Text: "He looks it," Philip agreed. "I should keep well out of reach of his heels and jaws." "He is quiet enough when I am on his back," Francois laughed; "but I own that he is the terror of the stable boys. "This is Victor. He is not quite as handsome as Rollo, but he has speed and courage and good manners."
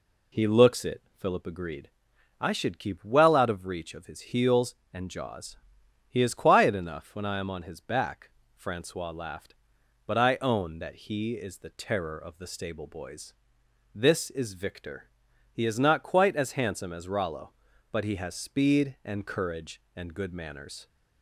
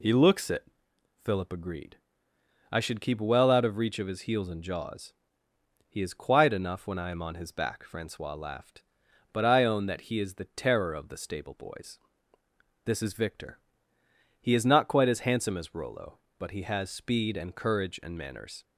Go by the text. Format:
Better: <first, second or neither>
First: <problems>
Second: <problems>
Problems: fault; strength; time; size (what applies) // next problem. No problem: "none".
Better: first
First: none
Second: skips "good"; at 18.1 s